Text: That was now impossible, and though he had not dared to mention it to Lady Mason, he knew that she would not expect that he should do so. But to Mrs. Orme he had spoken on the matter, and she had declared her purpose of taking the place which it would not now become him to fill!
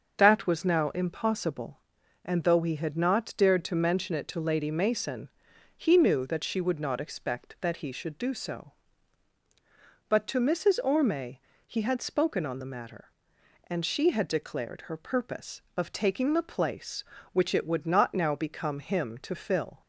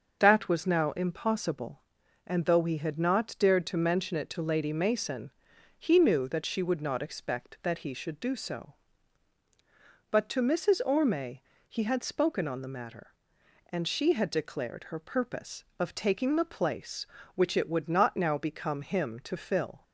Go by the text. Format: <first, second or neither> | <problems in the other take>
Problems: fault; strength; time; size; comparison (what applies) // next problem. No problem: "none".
neither | starts louder than the rest; the same in both // pauses between "Orme" and "he"; slight; the same in both